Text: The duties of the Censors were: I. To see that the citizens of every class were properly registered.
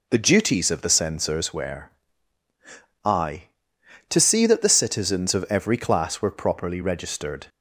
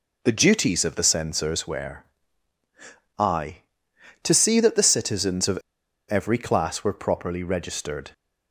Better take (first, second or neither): first